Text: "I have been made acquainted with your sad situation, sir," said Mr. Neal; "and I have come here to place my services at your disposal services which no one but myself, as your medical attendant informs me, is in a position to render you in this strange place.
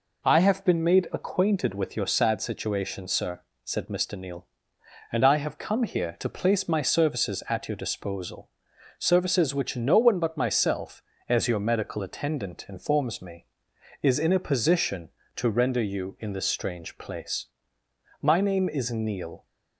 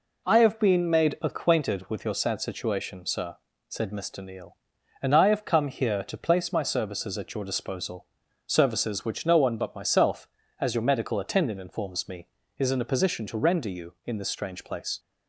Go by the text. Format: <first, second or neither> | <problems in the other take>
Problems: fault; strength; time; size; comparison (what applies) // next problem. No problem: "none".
second | pauses between "disposal" and "services"; noticeable; at 8.5 s; 0.48 s long; also in the second // goes on to say "My name is Neal"; noticeable; from 18.1 s on; 1.2 s long